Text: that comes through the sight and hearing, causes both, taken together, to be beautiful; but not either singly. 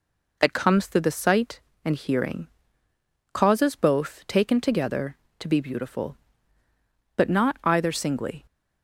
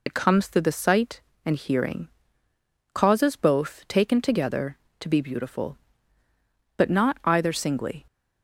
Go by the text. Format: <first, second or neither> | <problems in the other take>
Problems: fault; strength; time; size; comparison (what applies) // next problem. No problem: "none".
first | loses the start of "that"; at 0.0 s; 65 ms